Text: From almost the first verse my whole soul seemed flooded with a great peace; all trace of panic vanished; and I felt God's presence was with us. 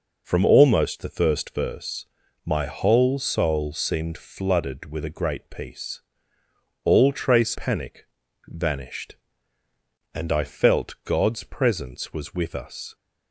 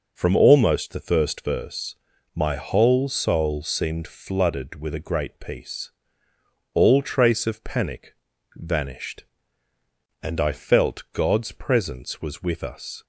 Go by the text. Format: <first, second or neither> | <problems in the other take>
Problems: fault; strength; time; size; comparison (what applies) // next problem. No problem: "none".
second | pauses between "verse" and "my"; at 2.0 s; 0.38 s long; also in the second // skips "of"; at 7.5 s // pauses between "panic" and "vanished"; at 8.0 s; 0.40 s long; also in the second